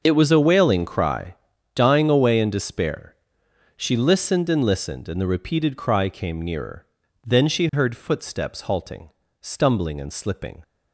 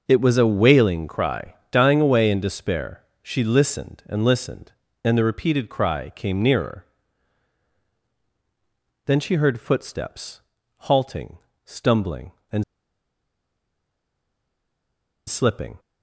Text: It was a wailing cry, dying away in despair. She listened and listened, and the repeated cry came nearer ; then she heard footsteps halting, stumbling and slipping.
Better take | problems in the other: first | pauses between "footsteps" and "halting"; slight; at 10.4 s; 0.34 s long // pauses between "and" and "slipping"; strong; at 12.6 s; 2.6 s long

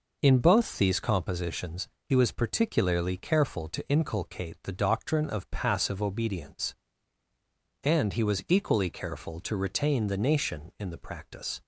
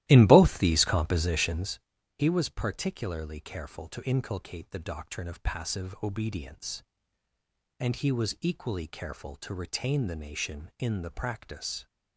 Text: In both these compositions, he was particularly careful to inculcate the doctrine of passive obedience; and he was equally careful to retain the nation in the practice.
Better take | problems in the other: first | starts louder than the rest; strong; until 1.9 s; 15 dB

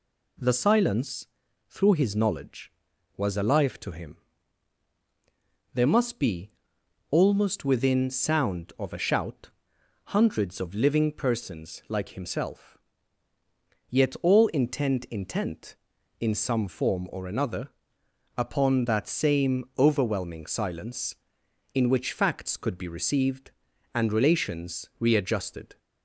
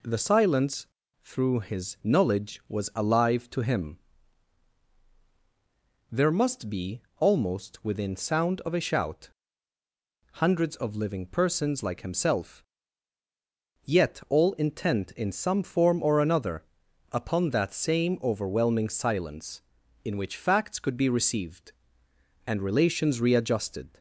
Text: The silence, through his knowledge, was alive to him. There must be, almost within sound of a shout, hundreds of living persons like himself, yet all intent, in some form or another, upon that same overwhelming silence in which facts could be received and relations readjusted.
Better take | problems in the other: second | says "intent" twice; at 15.0 s

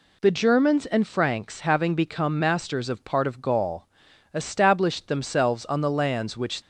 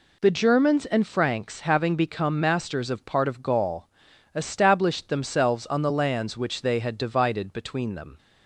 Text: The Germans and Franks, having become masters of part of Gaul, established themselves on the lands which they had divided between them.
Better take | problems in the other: second | stops before "they had divided between them"; at 6.6 s

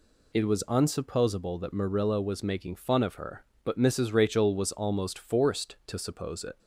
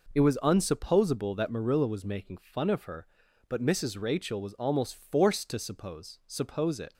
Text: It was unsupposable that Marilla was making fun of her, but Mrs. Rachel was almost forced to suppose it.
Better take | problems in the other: first | says "suppose" twice; at 6.2 s

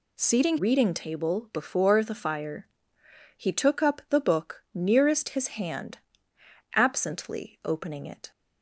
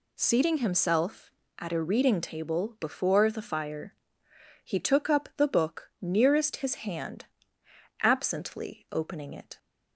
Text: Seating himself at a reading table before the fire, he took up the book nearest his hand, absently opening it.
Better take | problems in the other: second | skips "himself at a"; at 0.5 s

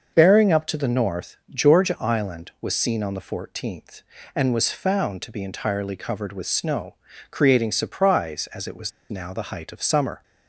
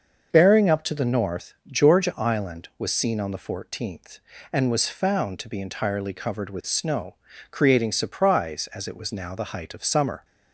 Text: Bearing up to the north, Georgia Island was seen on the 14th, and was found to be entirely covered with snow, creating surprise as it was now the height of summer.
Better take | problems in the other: second | starts louder than the rest; until 1.1 s; 6.5 dB; also in the second // pauses between "was" and "now"; slight; at 8.9 s; 0.19 s long

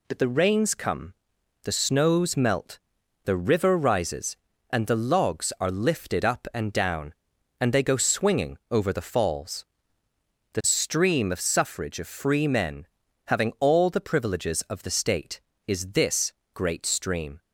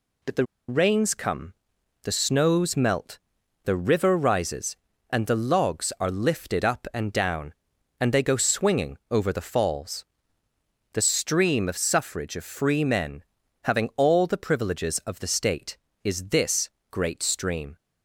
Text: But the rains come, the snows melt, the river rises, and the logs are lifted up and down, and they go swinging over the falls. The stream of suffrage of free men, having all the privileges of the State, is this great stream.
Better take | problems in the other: first | pauses between "the" and "rains"; slight; at 0.4 s; 0.22 s long // pauses between "this" and "great"; slight; at 16.6 s; 0.22 s long; slight in the first

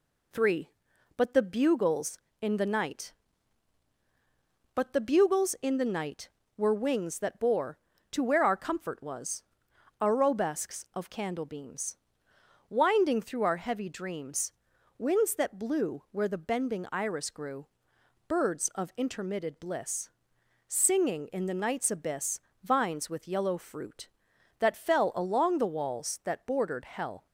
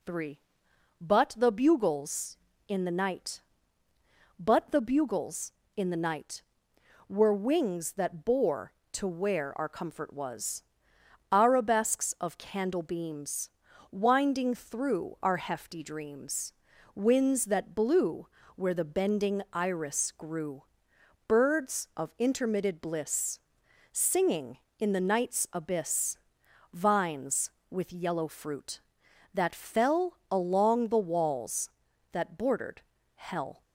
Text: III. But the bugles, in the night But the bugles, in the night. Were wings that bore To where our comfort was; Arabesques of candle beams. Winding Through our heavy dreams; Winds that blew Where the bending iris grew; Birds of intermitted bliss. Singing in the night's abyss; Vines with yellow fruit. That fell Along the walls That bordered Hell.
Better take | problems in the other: first | says "hefty" for "heavy"; at 15.3 s // pauses between "blew" and "Where"; slight; at 18.2 s; 0.30 s long // pauses between "bordered" and "Hell"; slight; at 32.8 s; 0.34 s long

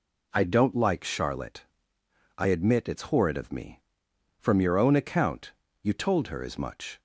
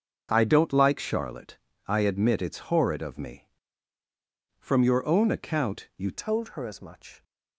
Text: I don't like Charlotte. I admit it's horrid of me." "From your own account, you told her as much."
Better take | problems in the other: first | starts louder than the rest; until 1.3 s; 6.5 dB // changes voice at "told"; from 6.1 s on; 1.1 s long

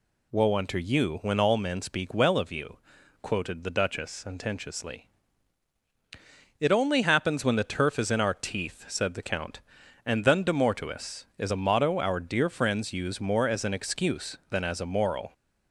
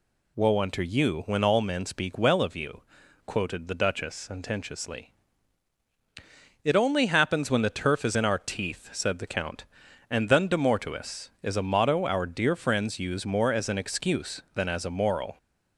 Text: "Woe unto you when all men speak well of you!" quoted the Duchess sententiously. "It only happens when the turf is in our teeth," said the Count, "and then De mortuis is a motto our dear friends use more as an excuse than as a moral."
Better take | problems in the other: neither | none

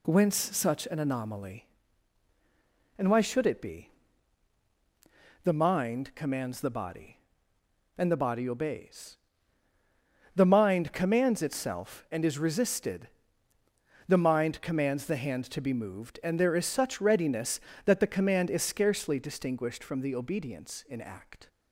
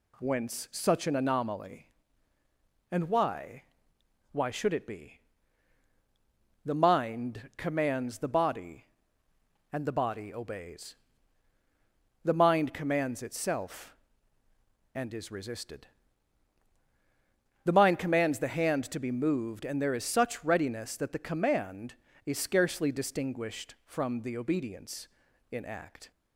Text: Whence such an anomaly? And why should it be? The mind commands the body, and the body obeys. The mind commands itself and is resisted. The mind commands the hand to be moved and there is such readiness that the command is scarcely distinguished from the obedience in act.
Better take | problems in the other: first | says "why" twice; at 4.3 s

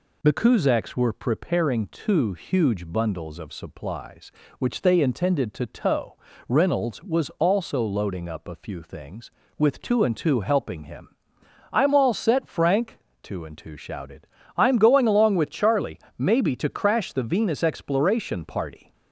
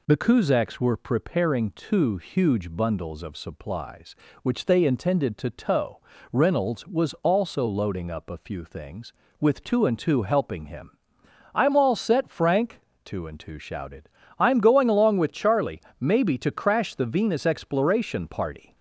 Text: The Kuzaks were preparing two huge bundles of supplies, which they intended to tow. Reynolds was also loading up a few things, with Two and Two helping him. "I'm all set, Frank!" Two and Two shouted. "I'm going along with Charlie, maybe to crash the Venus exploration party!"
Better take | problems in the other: neither | none

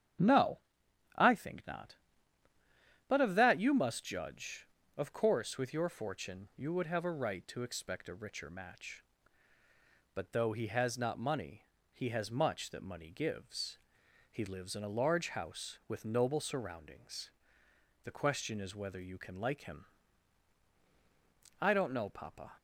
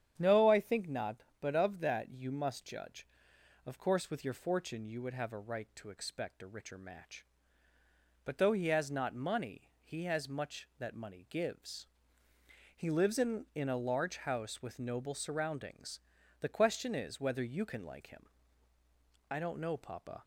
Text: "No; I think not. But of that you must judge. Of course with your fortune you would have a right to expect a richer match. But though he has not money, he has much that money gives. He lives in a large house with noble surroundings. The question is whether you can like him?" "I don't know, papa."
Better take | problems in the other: first | starts louder than the rest; strong; until 1.2 s; 8.5 dB; strong in the first // says "in" twice; at 13.5 s

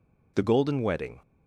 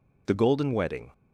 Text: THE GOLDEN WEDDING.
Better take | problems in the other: neither | none

